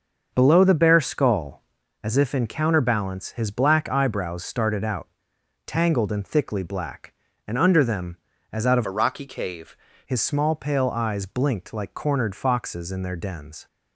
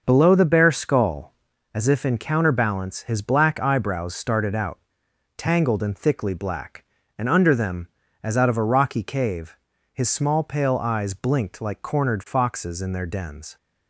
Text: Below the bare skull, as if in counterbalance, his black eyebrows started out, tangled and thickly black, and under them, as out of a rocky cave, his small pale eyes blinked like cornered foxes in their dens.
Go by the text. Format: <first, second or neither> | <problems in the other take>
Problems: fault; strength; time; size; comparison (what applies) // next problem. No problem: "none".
second | starts louder than the rest; until 1.3 s; 6.5 dB; noticeable in the second // changes voice from "a" to "cave"; from 8.8 to 9.7 s; 0.9 s long